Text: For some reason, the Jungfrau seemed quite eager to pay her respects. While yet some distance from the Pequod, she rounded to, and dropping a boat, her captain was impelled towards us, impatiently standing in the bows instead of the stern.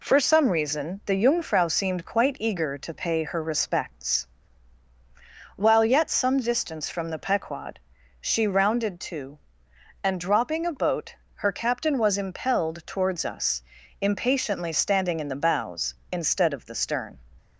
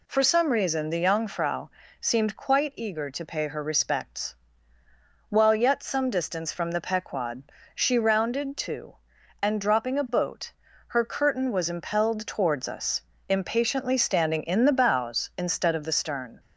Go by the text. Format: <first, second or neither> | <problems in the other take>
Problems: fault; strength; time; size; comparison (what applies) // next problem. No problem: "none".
first | pauses between "Jungfrau" and "seemed"; slight; at 1.6 s; 0.32 s long // says "curtain" for "captain"; at 11.0 s